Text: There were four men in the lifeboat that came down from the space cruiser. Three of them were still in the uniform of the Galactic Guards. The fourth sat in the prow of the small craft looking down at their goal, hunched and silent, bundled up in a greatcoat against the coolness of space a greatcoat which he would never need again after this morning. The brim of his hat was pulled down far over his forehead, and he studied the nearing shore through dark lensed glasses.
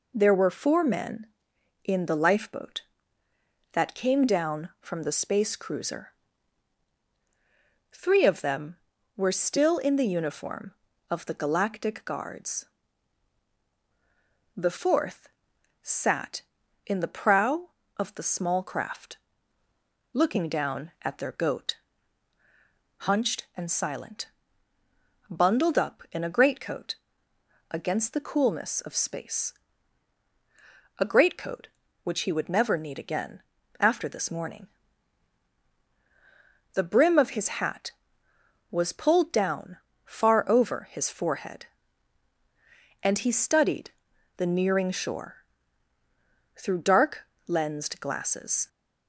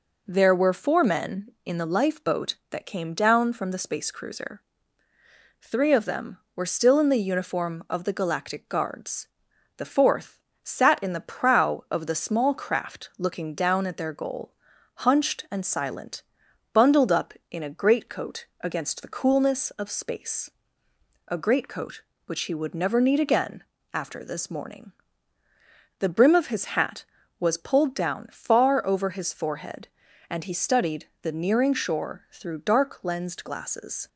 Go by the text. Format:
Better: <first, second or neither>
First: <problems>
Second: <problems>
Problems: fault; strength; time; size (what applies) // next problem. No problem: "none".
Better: second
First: pauses between "fourth" and "sat"; noticeable; at 15.2 s; 0.52 s long // pauses between "craft" and "looking"; noticeable; at 19.1 s; 0.98 s long // says "goat" for "goal"; at 21.3 s // pauses between "greatcoat" and "against"; noticeable; at 26.9 s; 0.78 s long // pauses between "space" and "a"; strong; at 29.5 s; 1.4 s long // pauses between "again" and "after"; at 33.3 s; 0.40 s long // pauses between "down" and "far"; slight; at 39.7 s; 0.28 s long // pauses between "studied" and "the"; noticeable; at 43.8 s; 0.46 s long // pauses between "shore" and "through"; at 45.3 s; 1.1 s long // pauses between "dark" and "lensed"; slight; at 47.2 s; 0.24 s long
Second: pauses between "fourth" and "sat"; slight; at 10.3 s; 0.24 s long // pauses between "greatcoat" and "against"; slight; at 18.4 s; 0.16 s long // pauses between "space" and "a"; noticeable; at 20.4 s; 0.78 s long // pauses between "again" and "after"; slight; at 23.6 s; 0.28 s long // pauses between "studied" and "the"; slight; at 31.0 s; 0.16 s long